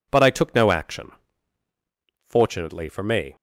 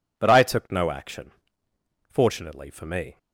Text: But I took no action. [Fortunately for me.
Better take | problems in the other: neither | none

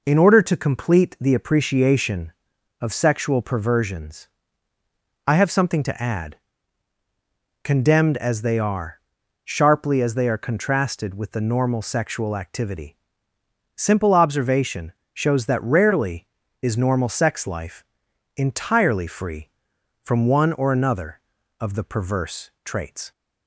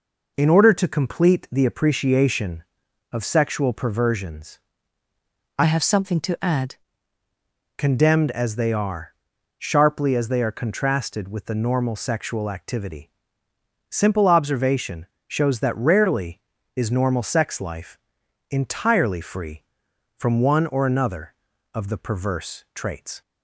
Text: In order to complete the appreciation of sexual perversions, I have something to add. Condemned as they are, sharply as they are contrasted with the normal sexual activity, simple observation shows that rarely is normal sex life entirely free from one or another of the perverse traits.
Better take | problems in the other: first | changes voice from "have" to "add"; from 5.6 to 6.7 s; 1.1 s long // pauses between "observation" and "shows"; slight; at 15.0 s; 0.22 s long; slight in the first // pauses between "life" and "entirely"; noticeable; at 17.9 s; 0.50 s long; noticeable in the first

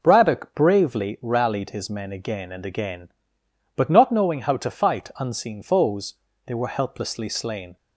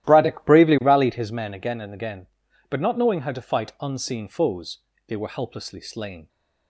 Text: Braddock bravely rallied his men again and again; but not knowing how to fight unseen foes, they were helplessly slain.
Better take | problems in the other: first | starts louder than the rest; strong; until 1.3 s; 13 dB

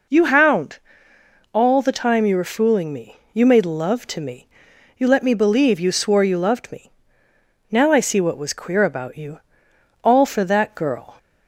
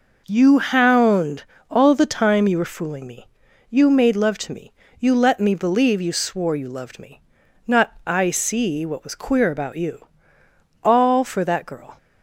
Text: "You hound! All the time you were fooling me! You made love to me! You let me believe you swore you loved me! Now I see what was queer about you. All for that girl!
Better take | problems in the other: first | says "Not" for "Now"; at 7.6 s

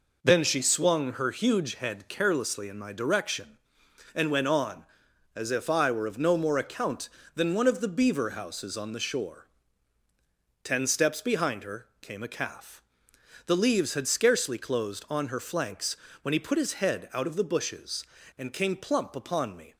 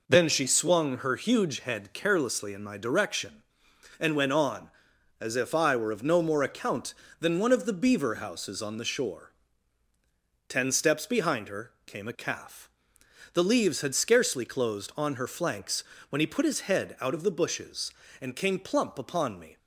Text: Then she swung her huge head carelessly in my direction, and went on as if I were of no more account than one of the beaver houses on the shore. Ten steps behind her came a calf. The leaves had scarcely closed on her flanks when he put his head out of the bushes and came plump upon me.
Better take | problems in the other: neither | pauses between "flanks" and "when"; slight; the same in both

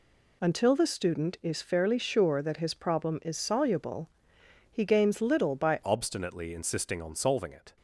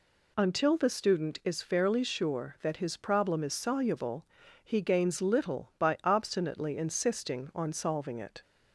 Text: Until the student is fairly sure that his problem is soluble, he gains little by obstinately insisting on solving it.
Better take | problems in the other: second | changes voice at "obstinately"; from 5.8 s on; 1.9 s long

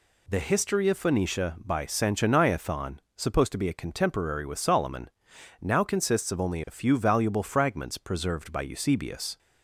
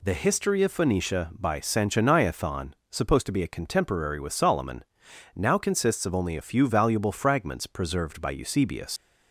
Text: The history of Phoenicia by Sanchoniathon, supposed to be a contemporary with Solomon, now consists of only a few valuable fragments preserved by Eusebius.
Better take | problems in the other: first | leaves "Eusebius" unfinished; at 8.9 s; 105 ms

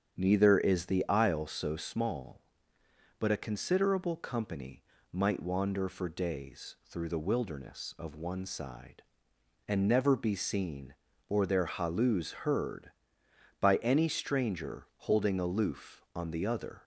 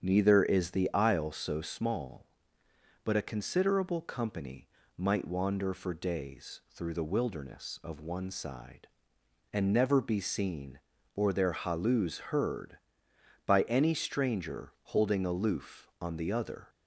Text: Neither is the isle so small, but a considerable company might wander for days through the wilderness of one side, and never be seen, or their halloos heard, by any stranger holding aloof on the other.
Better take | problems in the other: neither | starts louder than the rest; strong; the same in both // pauses between "company" and "might"; slight; the same in both

